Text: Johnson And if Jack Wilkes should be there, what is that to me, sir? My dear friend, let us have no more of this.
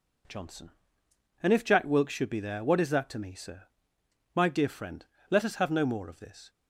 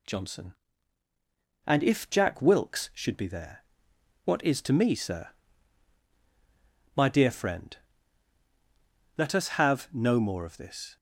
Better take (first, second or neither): first